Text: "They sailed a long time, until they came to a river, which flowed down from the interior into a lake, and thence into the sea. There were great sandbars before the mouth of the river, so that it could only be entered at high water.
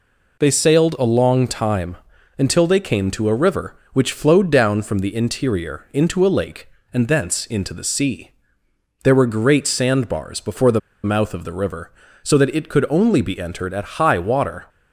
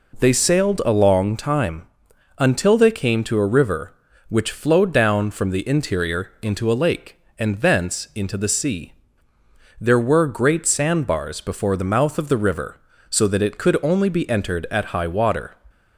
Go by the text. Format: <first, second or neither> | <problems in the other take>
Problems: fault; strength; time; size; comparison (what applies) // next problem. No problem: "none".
second | pauses between "the" and "mouth"; slight; at 10.7 s; 0.24 s long